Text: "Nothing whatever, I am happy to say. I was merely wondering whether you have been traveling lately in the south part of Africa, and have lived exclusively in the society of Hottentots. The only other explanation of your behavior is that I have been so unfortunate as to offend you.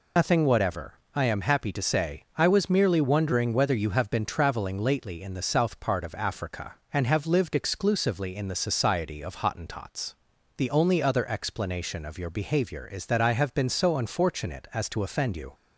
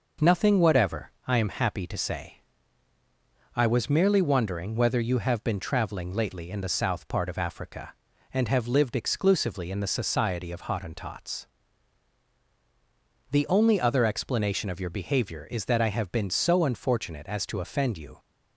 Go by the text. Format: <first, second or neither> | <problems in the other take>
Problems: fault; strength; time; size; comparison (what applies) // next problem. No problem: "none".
second | loses the start of "Nothing"; at 0.1 s; 115 ms